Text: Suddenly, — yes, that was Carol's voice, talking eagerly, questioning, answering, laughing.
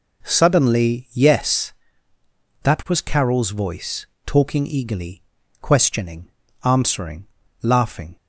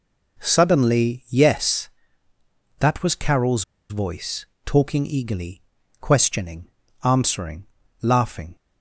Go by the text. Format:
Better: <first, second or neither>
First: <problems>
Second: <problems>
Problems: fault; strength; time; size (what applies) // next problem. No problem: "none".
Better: first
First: none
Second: pauses between "Carol's" and "voice"; slight; at 3.6 s; 0.26 s long